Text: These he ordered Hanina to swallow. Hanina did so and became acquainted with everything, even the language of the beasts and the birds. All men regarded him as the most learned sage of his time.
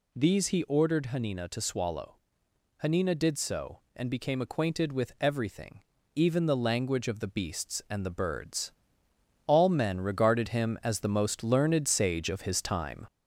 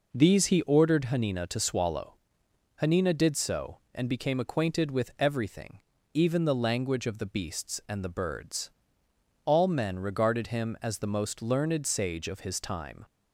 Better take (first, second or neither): second